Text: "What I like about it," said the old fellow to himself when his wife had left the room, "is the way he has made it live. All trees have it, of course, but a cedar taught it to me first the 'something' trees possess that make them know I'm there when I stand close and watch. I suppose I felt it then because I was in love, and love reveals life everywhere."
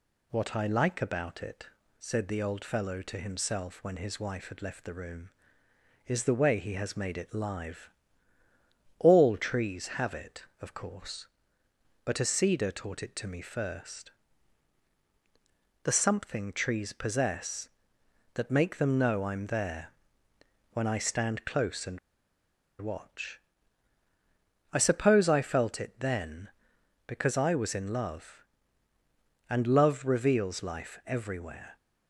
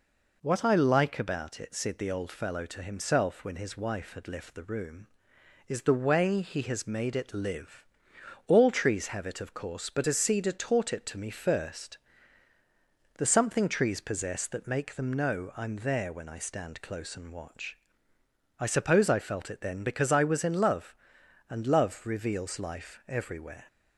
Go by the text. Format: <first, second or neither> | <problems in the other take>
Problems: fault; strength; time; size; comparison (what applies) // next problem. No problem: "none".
second | pauses between "first" and "the"; strong; at 14.1 s; 1.7 s long; also in the second // pauses between "there" and "when"; noticeable; at 19.8 s; 0.84 s long // pauses between "and" and "watch"; noticeable; at 21.9 s; 0.82 s long